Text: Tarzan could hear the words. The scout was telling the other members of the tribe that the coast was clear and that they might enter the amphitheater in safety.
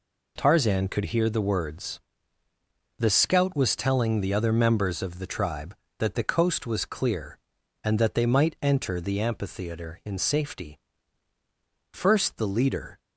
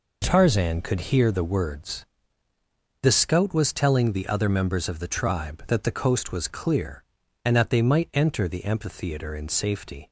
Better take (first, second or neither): second